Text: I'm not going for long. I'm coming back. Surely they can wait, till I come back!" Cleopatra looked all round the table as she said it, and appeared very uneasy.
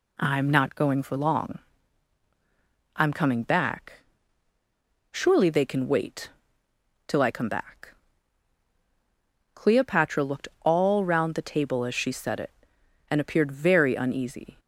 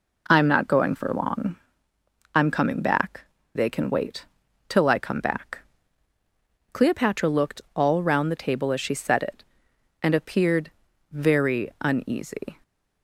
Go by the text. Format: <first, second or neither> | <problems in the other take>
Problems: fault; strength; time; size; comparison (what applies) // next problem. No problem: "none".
first | skips "Surely"; at 3.3 s // pauses between "appeared" and "very"; at 10.7 s; 0.40 s long